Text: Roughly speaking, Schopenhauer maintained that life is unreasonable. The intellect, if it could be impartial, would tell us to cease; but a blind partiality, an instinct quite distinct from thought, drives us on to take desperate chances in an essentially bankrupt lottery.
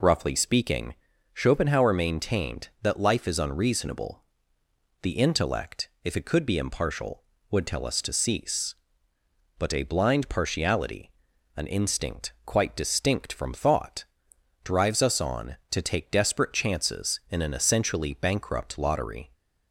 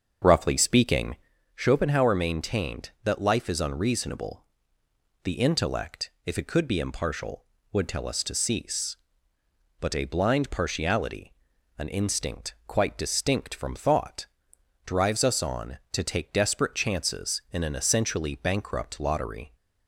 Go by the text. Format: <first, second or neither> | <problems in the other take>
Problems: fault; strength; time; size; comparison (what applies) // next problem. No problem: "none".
first | starts louder than the rest; until 1.4 s; 7 dB